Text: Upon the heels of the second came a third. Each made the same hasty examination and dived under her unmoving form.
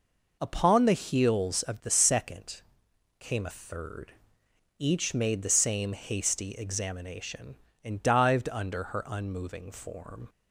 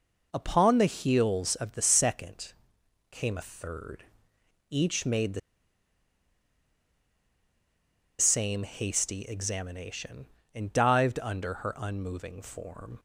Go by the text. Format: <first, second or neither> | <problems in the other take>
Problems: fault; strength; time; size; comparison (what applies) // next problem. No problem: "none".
first | pauses between "second" and "came"; noticeable; at 2.5 s; 0.58 s long; noticeable in the first // pauses between "the" and "same"; strong; at 5.3 s; 2.7 s long